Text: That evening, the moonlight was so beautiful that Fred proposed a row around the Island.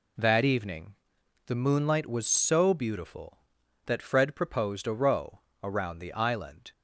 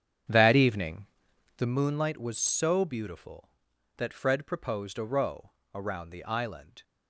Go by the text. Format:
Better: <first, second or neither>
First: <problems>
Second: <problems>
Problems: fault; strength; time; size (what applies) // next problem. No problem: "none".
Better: first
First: pauses between "row" and "around"; slight; at 5.3 s; 0.24 s long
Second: starts louder than the rest; strong; until 1.9 s; 8.5 dB // pauses between "row" and "around"; slight; at 5.5 s; 0.24 s long